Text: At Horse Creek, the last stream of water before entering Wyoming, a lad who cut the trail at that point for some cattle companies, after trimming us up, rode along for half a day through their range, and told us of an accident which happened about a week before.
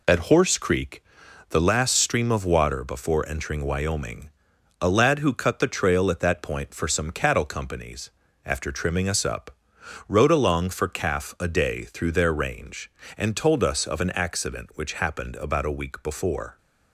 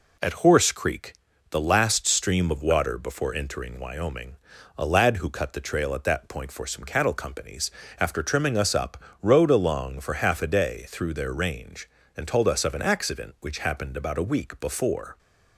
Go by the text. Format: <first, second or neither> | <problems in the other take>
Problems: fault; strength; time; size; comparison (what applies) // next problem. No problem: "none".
second | says "calf" for "half"; at 10.8 s